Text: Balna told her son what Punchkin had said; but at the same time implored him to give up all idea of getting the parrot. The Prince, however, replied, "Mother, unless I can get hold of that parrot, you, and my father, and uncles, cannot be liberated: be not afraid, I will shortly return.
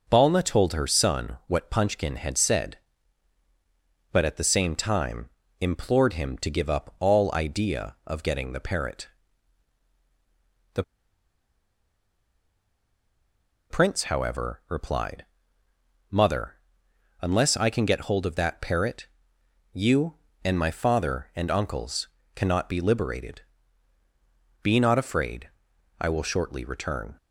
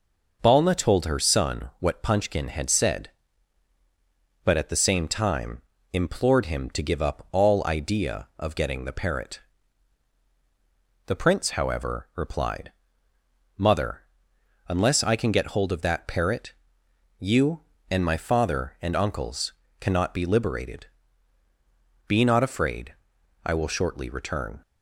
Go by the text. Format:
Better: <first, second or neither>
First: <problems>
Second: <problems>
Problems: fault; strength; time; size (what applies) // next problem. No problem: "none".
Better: second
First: pauses between "time" and "implored"; slight; at 5.2 s; 0.30 s long // pauses between "The" and "Prince"; strong; at 10.8 s; 2.8 s long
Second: pauses between "time" and "implored"; slight; at 5.6 s; 0.30 s long